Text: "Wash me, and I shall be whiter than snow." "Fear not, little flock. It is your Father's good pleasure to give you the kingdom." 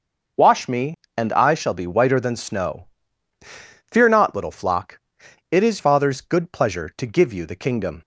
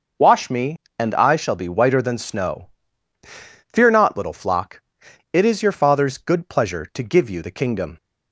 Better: second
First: skips "your"; at 5.7 s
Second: none

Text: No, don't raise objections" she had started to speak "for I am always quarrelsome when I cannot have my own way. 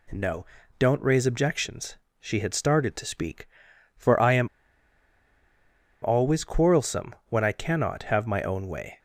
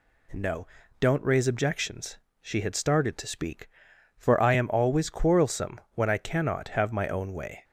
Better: second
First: pauses between "objections" and "she"; slight; at 1.9 s; 0.20 s long // pauses between "am" and "always"; strong; at 4.4 s; 1.5 s long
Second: pauses between "objections" and "she"; slight; at 2.1 s; 0.20 s long

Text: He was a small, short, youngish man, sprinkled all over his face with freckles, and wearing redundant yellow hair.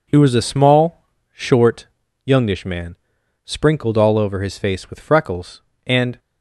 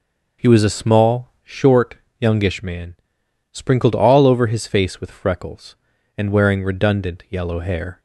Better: second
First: stops before "wearing redundant yellow hair"; at 6.1 s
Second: none

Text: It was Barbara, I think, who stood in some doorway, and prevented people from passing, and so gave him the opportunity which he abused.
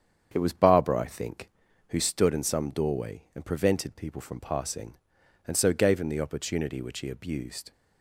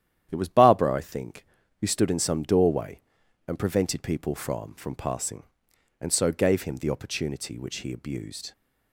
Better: first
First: starts louder than the rest; strong; until 1.3 s; 8 dB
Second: starts louder than the rest; strong; until 1.3 s; 10.5 dB // says "from" twice; at 4.7 s

